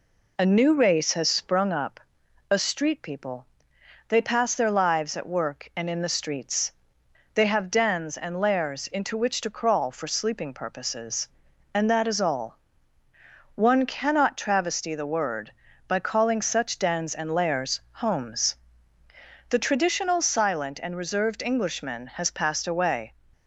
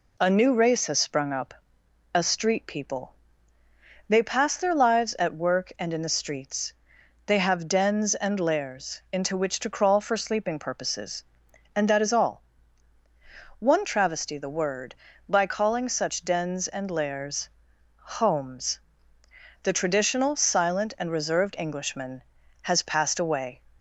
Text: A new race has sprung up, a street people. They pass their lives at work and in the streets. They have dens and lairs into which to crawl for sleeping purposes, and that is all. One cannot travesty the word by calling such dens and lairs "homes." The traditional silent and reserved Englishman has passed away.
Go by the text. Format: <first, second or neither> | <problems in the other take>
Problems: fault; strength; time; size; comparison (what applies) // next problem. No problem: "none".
first | skips "cannot"; at 13.8 s // pauses between "lairs" and "homes"; noticeable; at 17.4 s; 0.48 s long